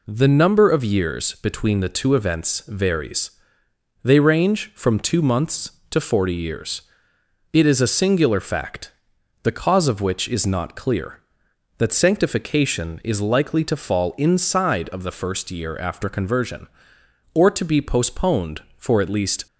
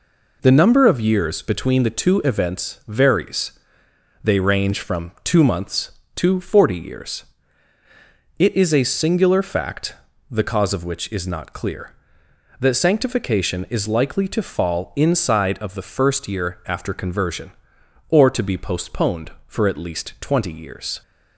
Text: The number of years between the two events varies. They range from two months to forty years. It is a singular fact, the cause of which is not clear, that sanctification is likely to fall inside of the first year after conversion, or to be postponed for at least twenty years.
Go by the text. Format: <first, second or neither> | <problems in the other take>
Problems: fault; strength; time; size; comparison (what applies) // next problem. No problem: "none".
second | stops before "twenty years"; at 19.4 s